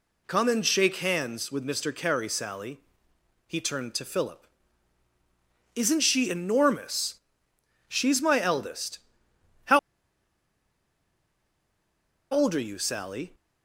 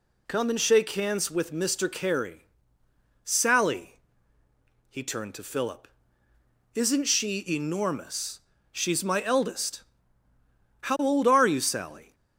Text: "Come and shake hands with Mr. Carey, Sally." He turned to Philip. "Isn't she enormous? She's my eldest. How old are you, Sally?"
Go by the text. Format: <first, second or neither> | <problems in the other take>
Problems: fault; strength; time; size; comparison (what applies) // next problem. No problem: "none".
second | pauses between "How" and "old"; strong; at 9.7 s; 2.5 s long